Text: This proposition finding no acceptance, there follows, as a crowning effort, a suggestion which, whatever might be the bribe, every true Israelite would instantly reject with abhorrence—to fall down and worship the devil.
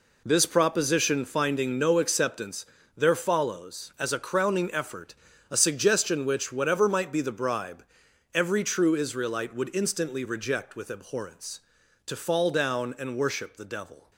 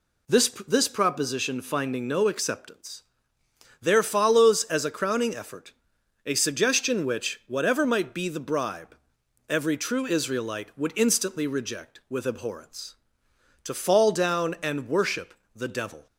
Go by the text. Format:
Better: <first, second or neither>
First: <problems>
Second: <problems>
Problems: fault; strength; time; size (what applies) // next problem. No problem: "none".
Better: first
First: none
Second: says "This" twice; at 0.6 s // pauses between "worship" and "the"; slight; at 15.3 s; 0.20 s long